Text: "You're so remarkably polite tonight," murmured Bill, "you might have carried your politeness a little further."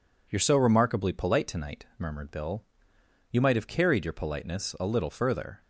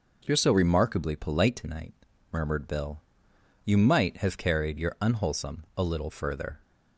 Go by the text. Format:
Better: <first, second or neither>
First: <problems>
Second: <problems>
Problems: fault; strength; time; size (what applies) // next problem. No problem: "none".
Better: first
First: none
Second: says "unwholesome" for "politeness"; at 5.0 s